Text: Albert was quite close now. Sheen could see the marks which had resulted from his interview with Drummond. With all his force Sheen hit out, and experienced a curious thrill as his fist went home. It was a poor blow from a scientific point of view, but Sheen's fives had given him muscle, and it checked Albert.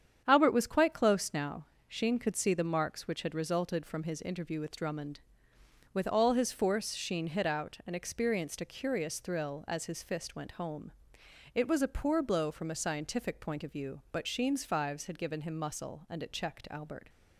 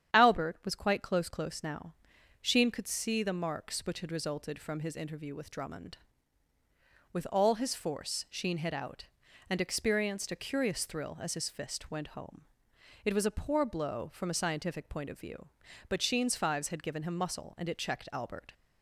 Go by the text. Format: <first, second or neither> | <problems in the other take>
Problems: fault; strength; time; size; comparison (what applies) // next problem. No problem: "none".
first | starts louder than the rest; strong; until 1.1 s; 9.5 dB; strong in the first // says "close" twice; at 1.2 s